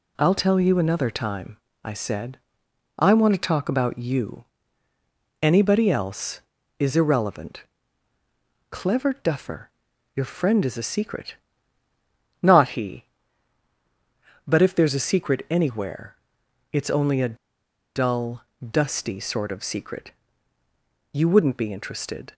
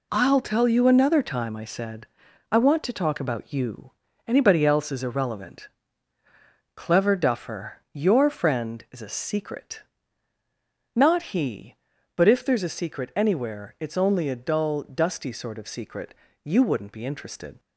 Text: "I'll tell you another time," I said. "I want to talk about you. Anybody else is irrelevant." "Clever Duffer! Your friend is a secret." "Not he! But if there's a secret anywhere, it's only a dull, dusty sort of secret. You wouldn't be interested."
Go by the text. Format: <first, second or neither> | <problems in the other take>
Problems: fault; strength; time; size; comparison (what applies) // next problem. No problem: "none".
second | pauses between "a" and "dull"; noticeable; at 17.3 s; 0.58 s long